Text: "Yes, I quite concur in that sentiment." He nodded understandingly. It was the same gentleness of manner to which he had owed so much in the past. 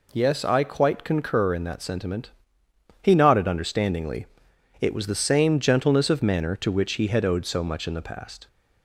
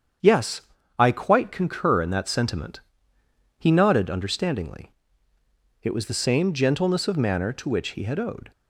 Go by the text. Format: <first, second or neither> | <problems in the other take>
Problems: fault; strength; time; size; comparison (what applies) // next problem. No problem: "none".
first | starts louder than the rest; strong; until 1.6 s; 8 dB // stops before "so much in the past"; at 8.5 s